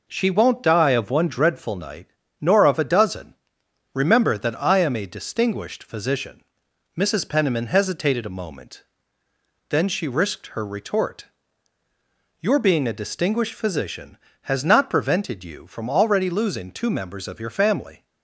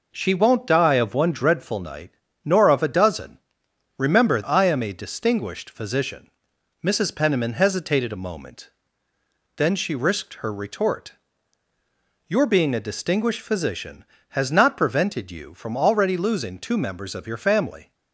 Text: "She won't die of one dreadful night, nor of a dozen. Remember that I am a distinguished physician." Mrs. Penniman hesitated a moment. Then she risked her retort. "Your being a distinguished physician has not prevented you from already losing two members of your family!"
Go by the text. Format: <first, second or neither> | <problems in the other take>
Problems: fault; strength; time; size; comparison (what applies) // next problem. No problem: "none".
first | skips "that"; at 4.4 s